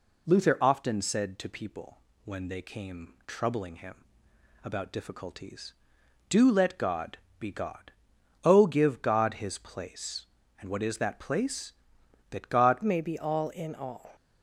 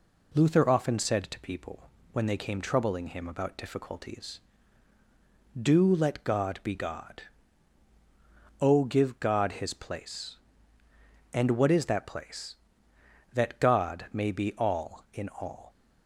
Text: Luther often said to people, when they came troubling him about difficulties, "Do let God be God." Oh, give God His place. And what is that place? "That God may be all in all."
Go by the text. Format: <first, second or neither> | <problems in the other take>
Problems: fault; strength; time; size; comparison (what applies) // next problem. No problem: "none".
second | pauses between "him" and "about"; noticeable; at 4.0 s; 0.58 s long // pauses between "God" and "be"; slight; at 7.1 s; 0.22 s long // changes voice at "may"; from 12.8 s on; 1.3 s long